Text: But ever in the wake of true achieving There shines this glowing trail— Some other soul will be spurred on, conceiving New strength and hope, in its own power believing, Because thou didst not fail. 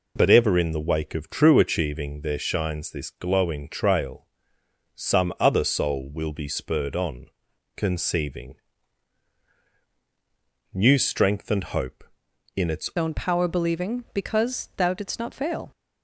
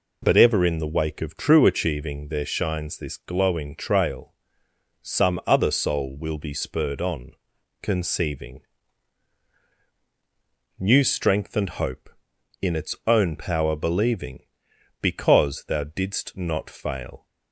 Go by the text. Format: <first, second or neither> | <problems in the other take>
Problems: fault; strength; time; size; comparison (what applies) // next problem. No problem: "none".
second | pauses between "conceiving" and "New"; strong; at 8.5 s; 2.1 s long; strong in the second // changes voice at "own"; from 12.9 s on; 2.8 s long